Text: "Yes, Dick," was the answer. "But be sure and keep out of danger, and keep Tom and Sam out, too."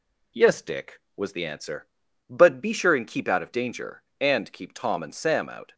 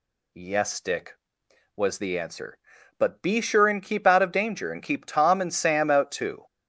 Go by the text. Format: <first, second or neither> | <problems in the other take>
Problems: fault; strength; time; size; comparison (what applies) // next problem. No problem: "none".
second | stops before "too"; at 5.7 s